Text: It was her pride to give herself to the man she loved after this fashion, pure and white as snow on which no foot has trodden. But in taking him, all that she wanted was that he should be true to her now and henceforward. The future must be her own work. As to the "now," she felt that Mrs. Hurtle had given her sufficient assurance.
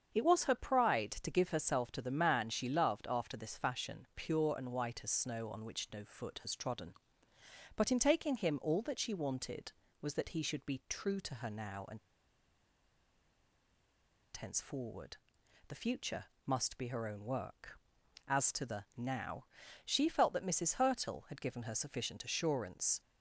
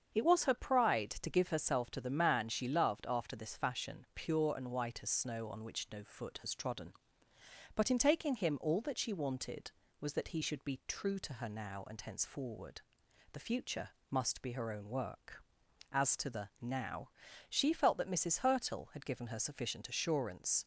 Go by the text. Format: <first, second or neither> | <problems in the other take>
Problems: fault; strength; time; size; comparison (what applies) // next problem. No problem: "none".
second | starts louder than the rest; strong; until 1.2 s; 7 dB; strong in the second // pauses between "and" and "henceforward"; strong; at 11.9 s; 2.3 s long // pauses between "future" and "must"; slight; at 16.2 s; 0.20 s long; slight in the second